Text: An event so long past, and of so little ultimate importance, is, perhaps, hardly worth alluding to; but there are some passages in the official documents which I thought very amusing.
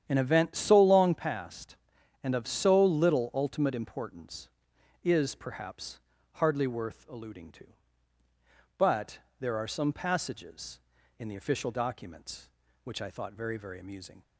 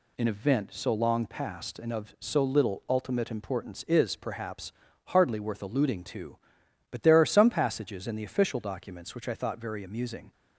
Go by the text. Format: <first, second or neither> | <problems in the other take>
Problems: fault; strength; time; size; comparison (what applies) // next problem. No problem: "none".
second | starts louder than the rest; strong; until 1.0 s; 9.5 dB // pauses between "but" and "there"; slight; at 9.1 s; 0.22 s long // says "very" twice; at 13.5 s